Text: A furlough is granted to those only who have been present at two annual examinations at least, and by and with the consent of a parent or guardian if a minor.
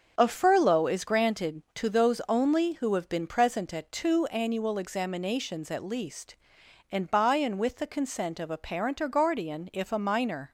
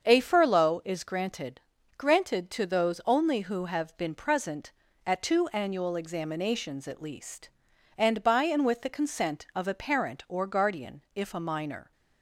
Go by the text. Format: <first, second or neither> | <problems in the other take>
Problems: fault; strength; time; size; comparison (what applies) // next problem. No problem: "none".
first | starts louder than the rest; until 1.0 s; 7 dB; also in the first // says "granted" twice; at 1.9 s